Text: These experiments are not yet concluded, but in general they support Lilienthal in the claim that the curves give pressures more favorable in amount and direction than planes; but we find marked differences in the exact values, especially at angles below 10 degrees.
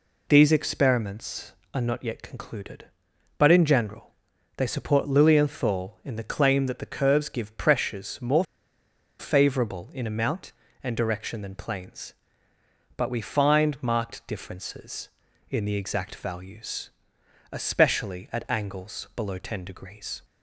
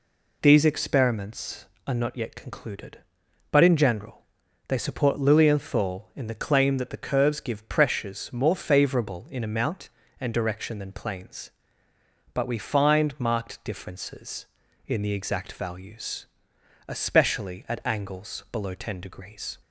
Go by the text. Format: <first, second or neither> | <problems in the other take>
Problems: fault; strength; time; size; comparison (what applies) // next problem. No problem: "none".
second | pauses between "general" and "they"; noticeable; at 4.1 s; 0.46 s long; noticeable in the second // pauses between "more" and "favorable"; noticeable; at 8.4 s; 0.75 s long